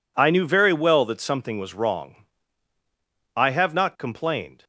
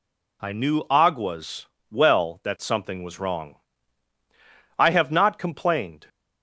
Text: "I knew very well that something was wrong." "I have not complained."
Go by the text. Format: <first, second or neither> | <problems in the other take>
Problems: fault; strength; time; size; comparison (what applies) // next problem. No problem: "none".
first | says "aguas" for "very"; at 0.8 s